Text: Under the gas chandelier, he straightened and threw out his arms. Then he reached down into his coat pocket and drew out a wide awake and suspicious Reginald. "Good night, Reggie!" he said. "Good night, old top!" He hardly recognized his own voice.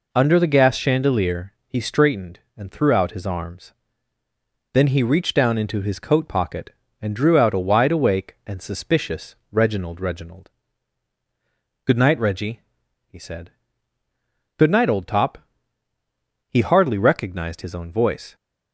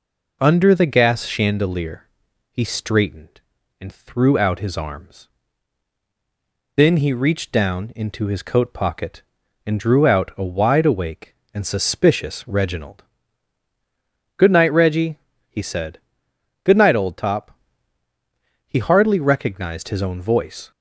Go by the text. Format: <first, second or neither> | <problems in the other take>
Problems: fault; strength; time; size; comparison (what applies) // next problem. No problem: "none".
second | pauses between "suspicious" and "Reginald"; slight; at 9.3 s; 0.16 s long // says "Reginald" twice; at 10.0 s